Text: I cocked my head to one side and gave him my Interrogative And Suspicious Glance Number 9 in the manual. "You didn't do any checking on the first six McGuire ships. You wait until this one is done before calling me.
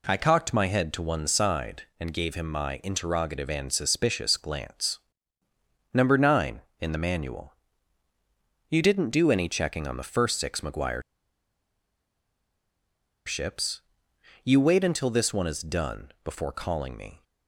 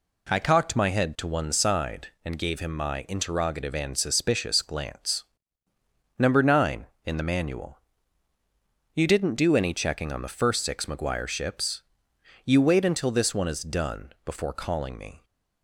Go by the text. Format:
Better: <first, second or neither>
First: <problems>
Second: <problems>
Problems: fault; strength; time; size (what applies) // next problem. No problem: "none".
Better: second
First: pauses between "Glance" and "Number"; noticeable; at 4.9 s; 0.96 s long // pauses between "McGuire" and "ships"; strong; at 11.0 s; 2.2 s long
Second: pauses between "Glance" and "Number"; noticeable; at 5.2 s; 0.96 s long